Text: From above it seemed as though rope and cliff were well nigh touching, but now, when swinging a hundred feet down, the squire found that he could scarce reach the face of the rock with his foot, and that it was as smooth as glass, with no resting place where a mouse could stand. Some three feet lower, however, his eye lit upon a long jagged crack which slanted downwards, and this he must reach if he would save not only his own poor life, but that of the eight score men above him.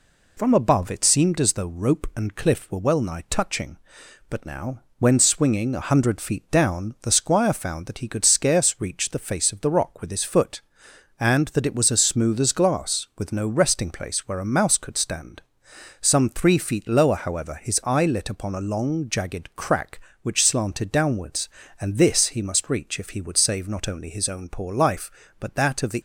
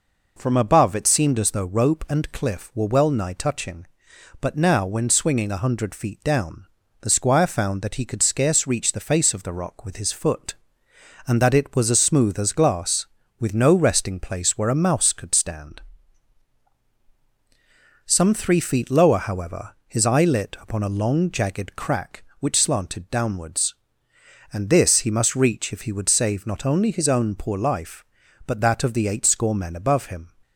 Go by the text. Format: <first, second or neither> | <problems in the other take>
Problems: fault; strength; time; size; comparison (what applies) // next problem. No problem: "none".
second | stops before "eight score men above him"; at 25.9 s